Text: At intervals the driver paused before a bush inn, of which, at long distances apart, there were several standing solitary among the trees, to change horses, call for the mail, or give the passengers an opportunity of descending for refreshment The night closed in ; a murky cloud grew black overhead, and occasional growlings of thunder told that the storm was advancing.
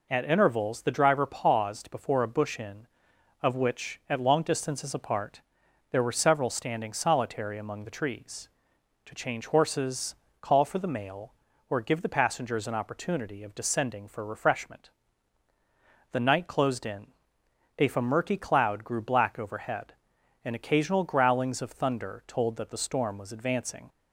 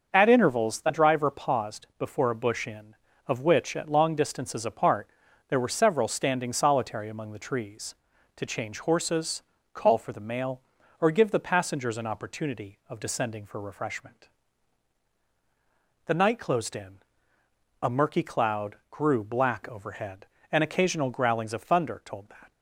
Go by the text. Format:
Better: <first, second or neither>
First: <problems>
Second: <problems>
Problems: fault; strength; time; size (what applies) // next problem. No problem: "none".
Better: first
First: pauses between "refreshment" and "The"; at 14.9 s; 1.2 s long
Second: starts louder than the rest; until 1.1 s; 6.5 dB // pauses between "refreshment" and "The"; strong; at 14.2 s; 1.7 s long // pauses between "cloud" and "grew"; slight; at 18.7 s; 0.16 s long // stops before "the storm was advancing"; at 22.5 s